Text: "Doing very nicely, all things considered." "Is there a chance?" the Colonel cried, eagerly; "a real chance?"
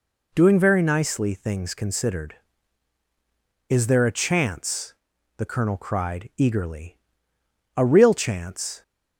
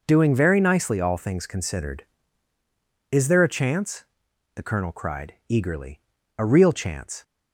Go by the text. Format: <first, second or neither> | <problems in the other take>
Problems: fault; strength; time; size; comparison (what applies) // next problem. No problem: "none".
second | skips "all"; at 1.3 s